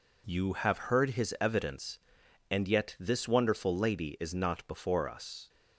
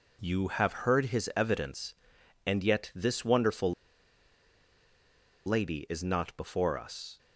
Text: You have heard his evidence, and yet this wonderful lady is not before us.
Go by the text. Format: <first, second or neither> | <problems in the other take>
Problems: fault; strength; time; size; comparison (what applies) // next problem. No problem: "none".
first | pauses between "wonderful" and "lady"; strong; at 3.7 s; 1.7 s long